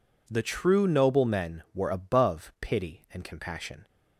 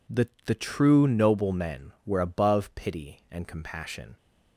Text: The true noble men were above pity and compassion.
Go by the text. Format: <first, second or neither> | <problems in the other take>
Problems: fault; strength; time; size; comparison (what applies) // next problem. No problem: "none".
first | says "The" twice; at 0.4 s